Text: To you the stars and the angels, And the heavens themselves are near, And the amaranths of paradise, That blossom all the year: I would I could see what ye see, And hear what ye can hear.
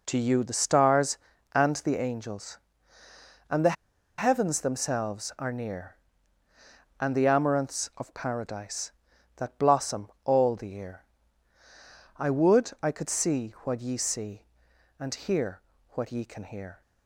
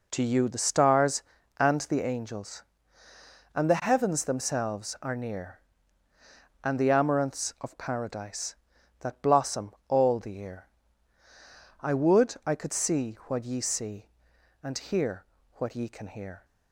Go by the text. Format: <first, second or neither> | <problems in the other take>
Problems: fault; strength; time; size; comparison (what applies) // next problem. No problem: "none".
second | pauses between "the" and "heavens"; at 3.7 s; 0.43 s long // pauses between "blossom" and "all"; slight; at 10.0 s; 0.16 s long; slight in the second // pauses between "hear" and "what"; slight; at 15.6 s; 0.30 s long; slight in the second